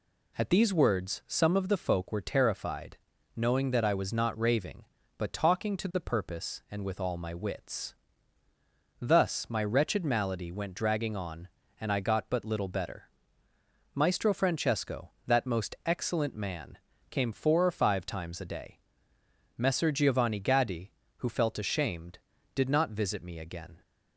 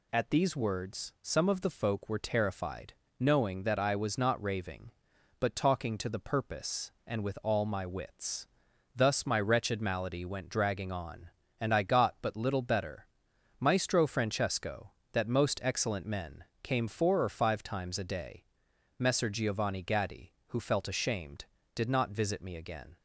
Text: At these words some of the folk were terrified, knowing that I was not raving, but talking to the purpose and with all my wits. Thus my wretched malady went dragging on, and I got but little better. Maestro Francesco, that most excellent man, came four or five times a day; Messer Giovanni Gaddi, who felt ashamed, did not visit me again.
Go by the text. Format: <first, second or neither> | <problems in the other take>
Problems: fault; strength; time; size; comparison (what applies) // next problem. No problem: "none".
first | says "men" for "man"; at 16.0 s